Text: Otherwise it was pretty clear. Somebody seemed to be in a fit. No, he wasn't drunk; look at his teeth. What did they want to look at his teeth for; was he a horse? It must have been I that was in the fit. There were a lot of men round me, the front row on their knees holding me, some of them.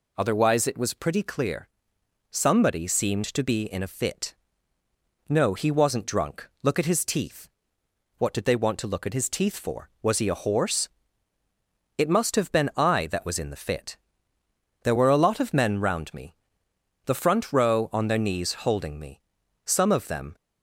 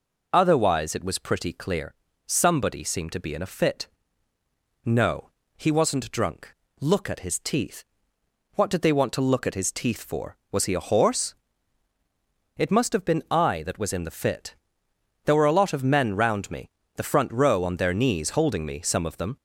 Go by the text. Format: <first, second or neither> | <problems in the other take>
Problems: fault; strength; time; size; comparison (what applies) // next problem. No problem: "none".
neither | none